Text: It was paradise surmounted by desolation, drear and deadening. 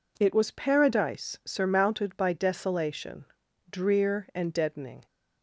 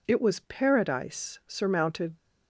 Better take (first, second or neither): first